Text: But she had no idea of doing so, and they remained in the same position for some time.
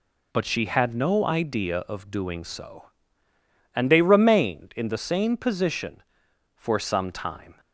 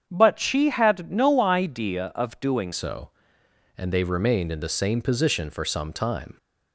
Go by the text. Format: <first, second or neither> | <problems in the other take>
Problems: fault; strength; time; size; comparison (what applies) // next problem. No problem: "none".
first | starts louder than the rest; strong; until 1.1 s; 7.5 dB // changes voice at "so"; from 2.7 s on; 3.6 s long